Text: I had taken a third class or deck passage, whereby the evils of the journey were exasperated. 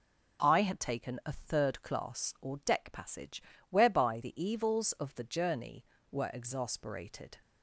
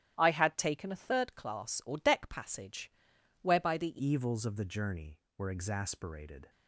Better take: first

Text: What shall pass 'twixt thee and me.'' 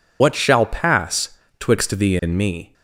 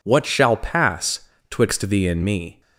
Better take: second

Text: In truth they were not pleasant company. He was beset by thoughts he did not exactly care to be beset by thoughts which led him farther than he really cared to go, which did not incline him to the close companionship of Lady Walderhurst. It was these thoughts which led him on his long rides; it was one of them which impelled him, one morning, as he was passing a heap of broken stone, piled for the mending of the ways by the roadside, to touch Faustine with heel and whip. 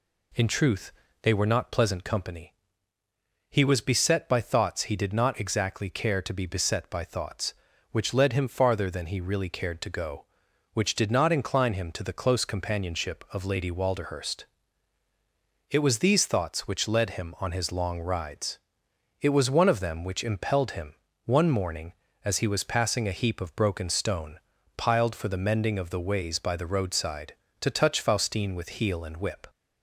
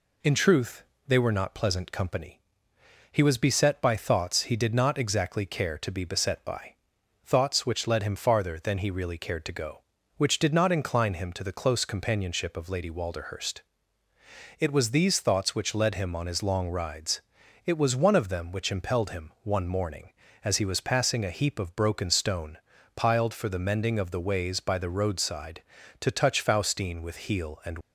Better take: first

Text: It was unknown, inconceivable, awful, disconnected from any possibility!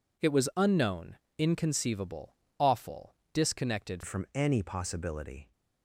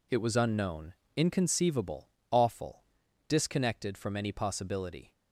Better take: second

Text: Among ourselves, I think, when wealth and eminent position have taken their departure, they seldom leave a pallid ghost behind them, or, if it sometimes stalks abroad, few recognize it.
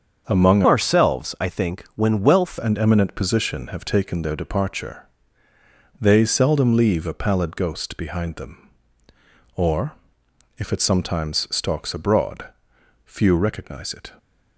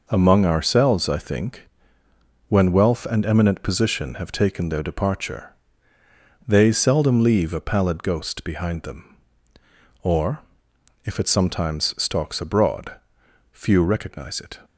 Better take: second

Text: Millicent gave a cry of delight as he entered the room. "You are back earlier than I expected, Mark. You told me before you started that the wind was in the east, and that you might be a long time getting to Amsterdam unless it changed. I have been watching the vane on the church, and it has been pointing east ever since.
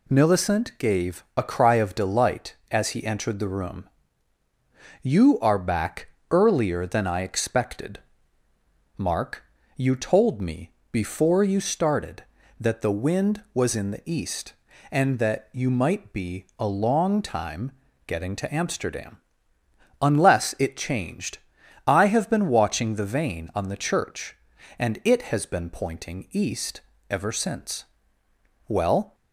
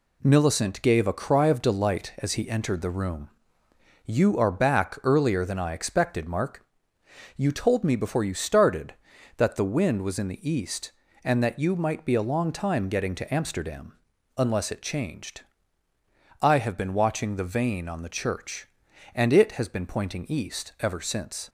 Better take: second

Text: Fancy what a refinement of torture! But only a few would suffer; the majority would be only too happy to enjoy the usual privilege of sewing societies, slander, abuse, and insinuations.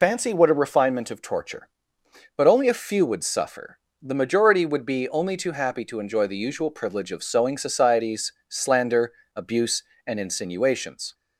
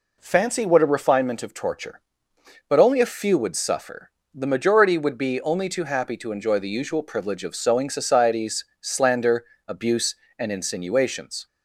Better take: second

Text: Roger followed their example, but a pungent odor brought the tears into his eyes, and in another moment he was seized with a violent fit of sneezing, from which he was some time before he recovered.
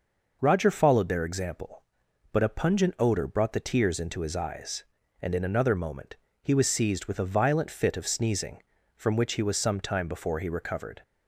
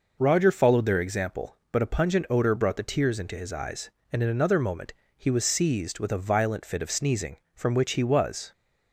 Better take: first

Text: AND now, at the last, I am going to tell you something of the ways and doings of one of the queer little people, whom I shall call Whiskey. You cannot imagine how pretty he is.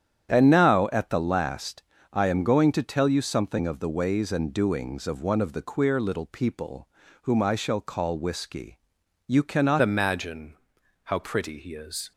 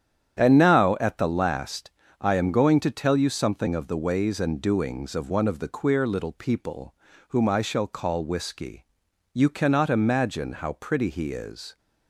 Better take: second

